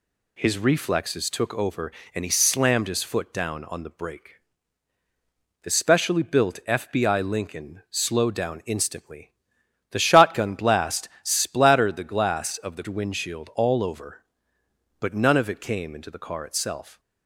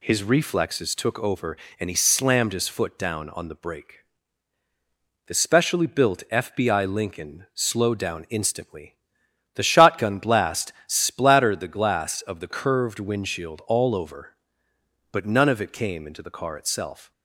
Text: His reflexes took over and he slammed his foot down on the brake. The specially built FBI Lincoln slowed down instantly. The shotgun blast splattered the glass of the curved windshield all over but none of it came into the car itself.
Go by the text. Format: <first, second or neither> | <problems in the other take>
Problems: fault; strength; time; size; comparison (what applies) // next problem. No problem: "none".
second | skips "curved"; at 12.8 s